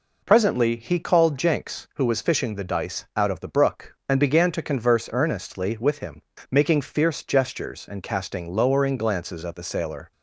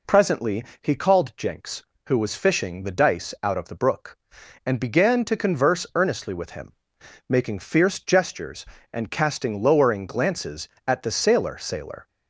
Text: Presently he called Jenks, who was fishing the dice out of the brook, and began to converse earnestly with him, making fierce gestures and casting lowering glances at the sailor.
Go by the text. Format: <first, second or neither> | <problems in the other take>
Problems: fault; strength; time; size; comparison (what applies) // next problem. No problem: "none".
first | pauses between "Presently" and "he"; slight; at 0.6 s; 0.20 s long // says "sailor" twice; at 11.5 s